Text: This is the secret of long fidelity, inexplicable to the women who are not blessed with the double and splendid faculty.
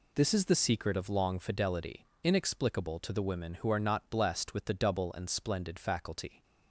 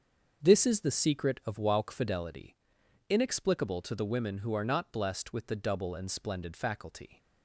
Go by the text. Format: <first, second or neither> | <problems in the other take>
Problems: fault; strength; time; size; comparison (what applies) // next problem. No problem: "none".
first | starts louder than the rest; until 1.4 s; 7 dB // says "wauk" for "long"; at 1.5 s